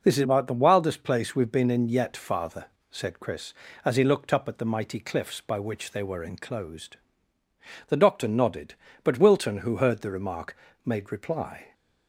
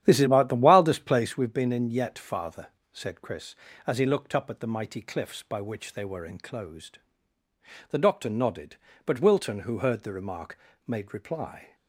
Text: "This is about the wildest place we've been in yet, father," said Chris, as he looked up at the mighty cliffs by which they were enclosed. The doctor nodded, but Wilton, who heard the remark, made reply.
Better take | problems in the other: first | starts louder than the rest; strong; until 1.4 s; 11 dB

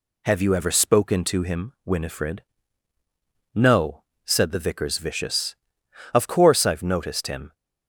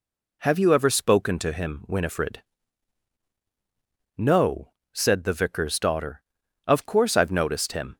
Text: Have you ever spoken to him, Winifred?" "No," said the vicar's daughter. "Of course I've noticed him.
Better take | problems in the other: second | says "vicious" for "daughter"; at 4.9 s

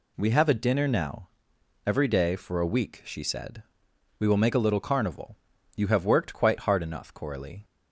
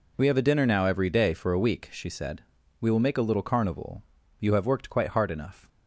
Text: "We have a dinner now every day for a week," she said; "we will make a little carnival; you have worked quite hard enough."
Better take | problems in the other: second | pauses between "now" and "every"; noticeable; at 1.2 s; 0.58 s long // goes on to say "Coralie"; from 7.1 s on; 0.50 s long

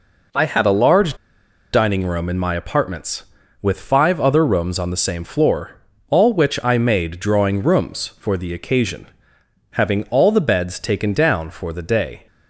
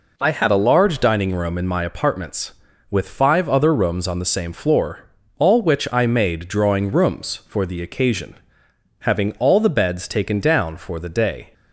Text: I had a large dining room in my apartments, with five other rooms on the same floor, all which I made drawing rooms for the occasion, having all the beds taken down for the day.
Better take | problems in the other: second | pauses between "large" and "dining"; noticeable; at 1.1 s; 0.59 s long

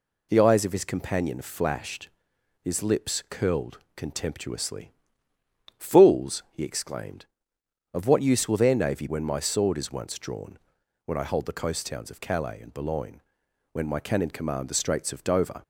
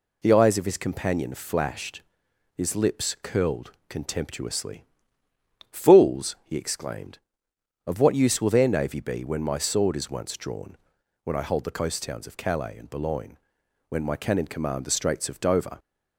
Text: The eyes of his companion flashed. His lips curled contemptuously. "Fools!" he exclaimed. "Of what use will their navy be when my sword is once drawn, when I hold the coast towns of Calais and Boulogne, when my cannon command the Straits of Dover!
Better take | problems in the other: second | pauses between "curled" and "contemptuously"; slight; at 3.7 s; 0.16 s long; slight in the second // skips "be"; at 9.0 s

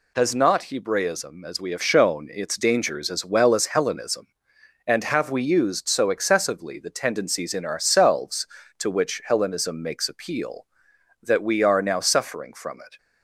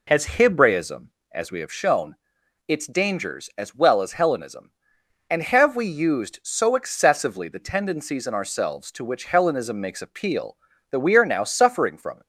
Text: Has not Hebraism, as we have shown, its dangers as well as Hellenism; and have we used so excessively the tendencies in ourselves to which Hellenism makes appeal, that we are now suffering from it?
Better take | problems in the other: first | skips "not"; at 0.2 s

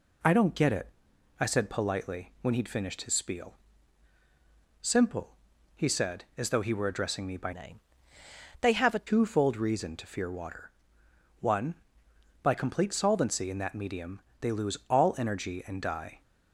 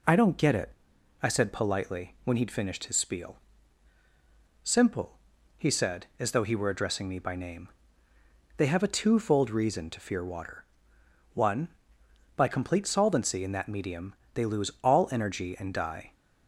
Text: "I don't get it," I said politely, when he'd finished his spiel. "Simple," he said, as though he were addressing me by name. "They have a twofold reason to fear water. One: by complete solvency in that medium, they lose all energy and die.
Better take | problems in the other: second | changes voice from "name" to "a"; from 7.5 to 9.0 s; 1.5 s long

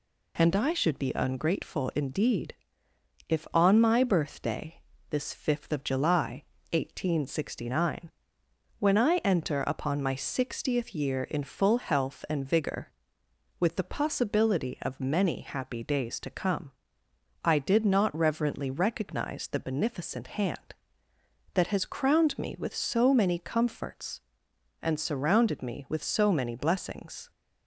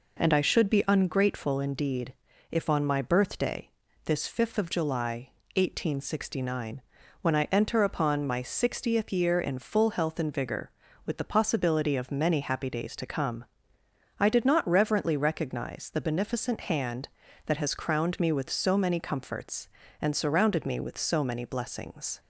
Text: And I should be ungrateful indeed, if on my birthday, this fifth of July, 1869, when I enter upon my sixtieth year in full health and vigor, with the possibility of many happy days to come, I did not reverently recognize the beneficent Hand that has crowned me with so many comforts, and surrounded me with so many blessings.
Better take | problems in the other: neither | none

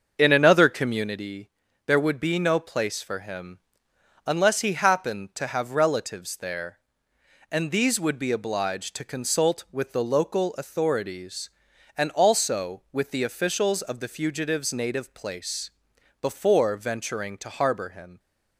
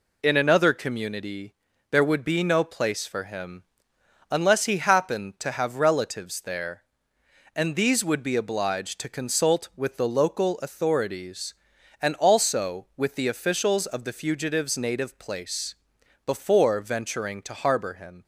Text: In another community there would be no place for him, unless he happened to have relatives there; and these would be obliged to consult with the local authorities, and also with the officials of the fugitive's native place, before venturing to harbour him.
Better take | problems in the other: second | starts louder than the rest; until 1.3 s; 7 dB // pauses between "community" and "there"; slight; at 1.4 s; 0.36 s long; slight in the second

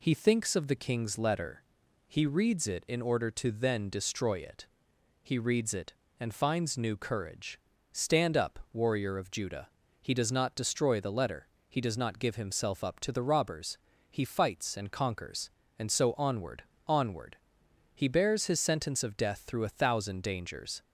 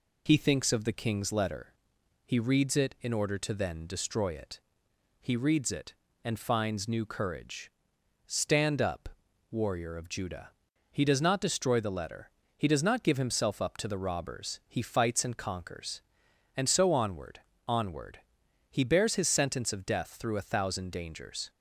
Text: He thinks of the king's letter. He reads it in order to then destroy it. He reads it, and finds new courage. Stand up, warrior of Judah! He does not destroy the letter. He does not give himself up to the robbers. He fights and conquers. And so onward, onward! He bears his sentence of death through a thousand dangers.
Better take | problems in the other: first | loses the start of "He"; at 0.2 s; 25 ms

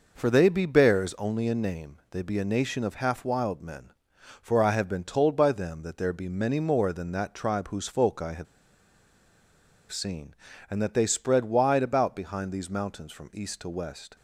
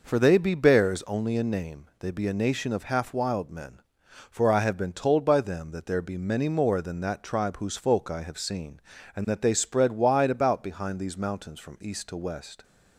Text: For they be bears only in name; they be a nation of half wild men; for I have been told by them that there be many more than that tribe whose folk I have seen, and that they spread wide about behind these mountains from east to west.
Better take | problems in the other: second | pauses between "have" and "seen"; strong; at 8.4 s; 1.4 s long

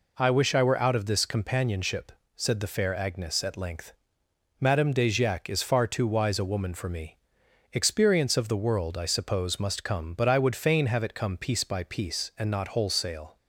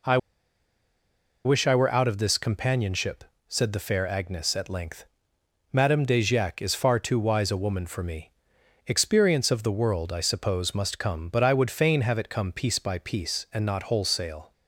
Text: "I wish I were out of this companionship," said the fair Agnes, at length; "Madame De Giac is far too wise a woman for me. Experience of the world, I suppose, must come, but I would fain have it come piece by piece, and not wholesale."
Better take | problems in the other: first | pauses between "I" and "wish"; strong; at 0.1 s; 1.2 s long

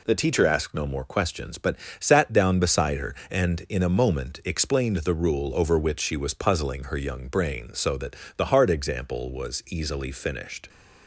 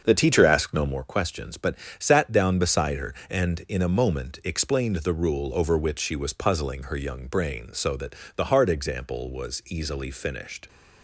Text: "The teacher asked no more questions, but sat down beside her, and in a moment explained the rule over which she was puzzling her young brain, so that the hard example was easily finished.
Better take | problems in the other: first | starts louder than the rest; until 1.0 s; 6.5 dB // pauses between "but" and "sat"; slight; at 1.7 s; 0.22 s long; slight in the first // pauses between "that" and "the"; slight; at 8.1 s; 0.22 s long; slight in the first

